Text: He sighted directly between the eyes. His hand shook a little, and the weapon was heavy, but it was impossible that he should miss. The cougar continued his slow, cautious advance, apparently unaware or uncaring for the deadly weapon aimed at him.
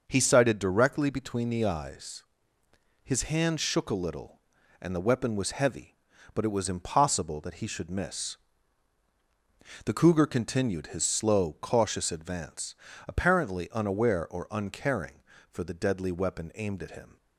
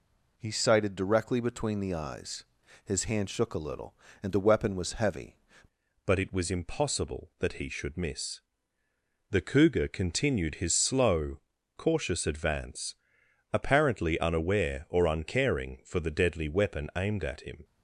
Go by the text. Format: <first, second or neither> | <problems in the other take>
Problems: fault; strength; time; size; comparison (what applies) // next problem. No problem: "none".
first | changes voice at "but"; from 6.0 s on; 11.6 s long